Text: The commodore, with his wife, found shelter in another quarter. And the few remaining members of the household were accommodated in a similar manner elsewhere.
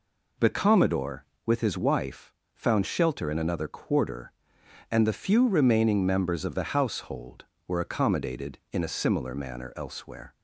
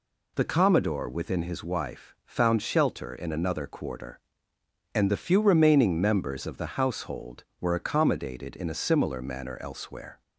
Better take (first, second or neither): first